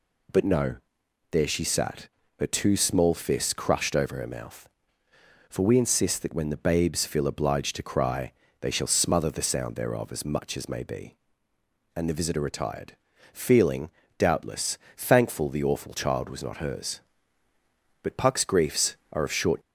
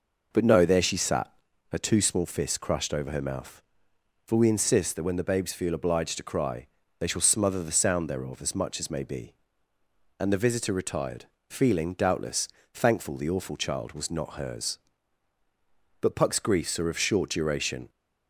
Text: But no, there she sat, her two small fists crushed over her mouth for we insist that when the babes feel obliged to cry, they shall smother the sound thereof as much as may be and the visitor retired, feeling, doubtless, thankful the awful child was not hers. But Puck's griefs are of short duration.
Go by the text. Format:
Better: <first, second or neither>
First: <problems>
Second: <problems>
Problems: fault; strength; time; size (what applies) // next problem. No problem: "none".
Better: second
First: stops before "duration"; at 19.6 s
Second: none